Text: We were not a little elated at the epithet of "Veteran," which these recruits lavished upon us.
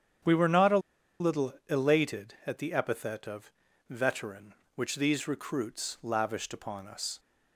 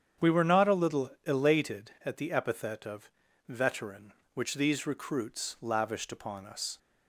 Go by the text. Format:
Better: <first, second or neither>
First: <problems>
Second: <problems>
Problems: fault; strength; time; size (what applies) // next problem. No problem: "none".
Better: second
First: starts louder than the rest; strong; until 1.8 s; 8.5 dB // pauses between "a" and "little"; at 0.7 s; 0.41 s long // pauses between "of" and "Veteran"; at 3.4 s; 0.40 s long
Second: starts louder than the rest; strong; until 1.3 s; 8.5 dB // pauses between "of" and "Veteran"; at 3.0 s; 0.40 s long